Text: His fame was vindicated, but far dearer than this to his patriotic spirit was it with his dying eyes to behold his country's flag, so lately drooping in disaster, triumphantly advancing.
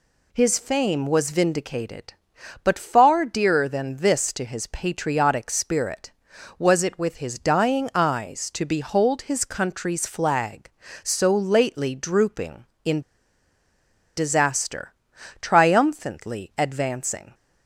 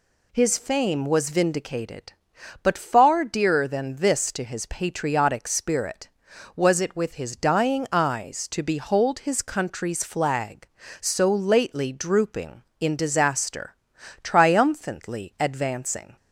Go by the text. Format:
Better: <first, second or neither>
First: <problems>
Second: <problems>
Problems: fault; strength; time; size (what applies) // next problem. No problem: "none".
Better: second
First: pauses between "in" and "disaster"; at 13.0 s; 1.1 s long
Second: none